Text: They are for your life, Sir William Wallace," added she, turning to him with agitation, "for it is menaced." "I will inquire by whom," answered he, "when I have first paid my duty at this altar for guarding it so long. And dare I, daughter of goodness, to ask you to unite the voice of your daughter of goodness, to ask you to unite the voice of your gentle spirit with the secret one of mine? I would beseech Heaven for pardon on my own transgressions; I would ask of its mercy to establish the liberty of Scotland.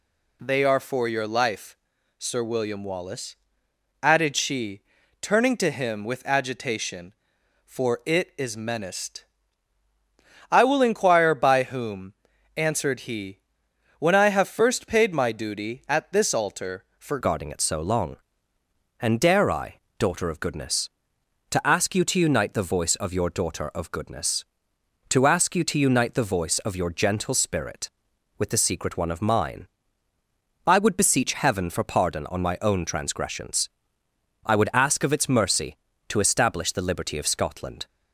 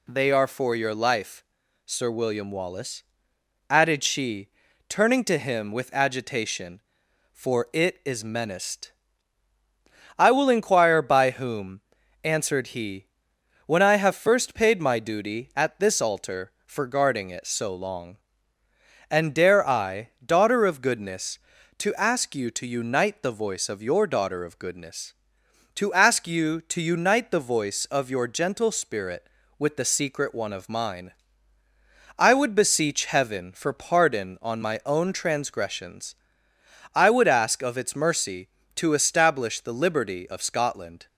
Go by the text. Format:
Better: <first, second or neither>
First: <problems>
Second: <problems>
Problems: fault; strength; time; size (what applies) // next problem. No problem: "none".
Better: second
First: changes voice at "guarding"; from 17.2 s on; 20.6 s long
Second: none